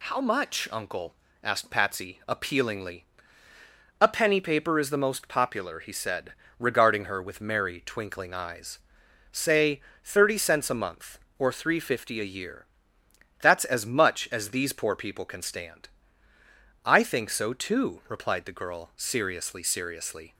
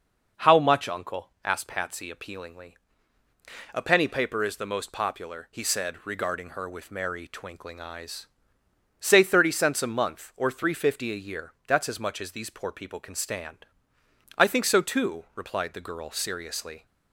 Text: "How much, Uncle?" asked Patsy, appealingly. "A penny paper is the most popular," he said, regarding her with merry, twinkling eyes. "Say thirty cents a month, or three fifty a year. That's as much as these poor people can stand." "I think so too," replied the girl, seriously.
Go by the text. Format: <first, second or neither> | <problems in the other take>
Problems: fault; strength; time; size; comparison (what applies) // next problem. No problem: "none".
second | pauses between "Say" and "thirty"; slight; at 9.7 s; 0.24 s long // says "seriously" twice; at 19.6 s